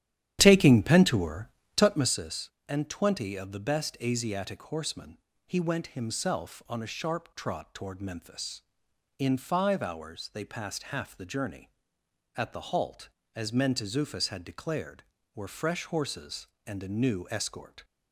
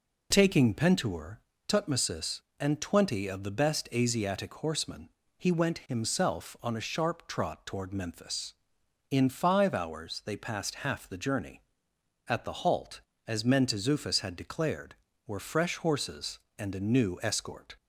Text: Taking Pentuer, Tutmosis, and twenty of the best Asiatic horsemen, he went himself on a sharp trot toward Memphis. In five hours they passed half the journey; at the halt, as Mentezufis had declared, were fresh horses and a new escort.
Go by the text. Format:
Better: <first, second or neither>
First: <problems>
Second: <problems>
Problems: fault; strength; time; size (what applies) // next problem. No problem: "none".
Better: second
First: starts louder than the rest; strong; until 2.3 s; 11 dB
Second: none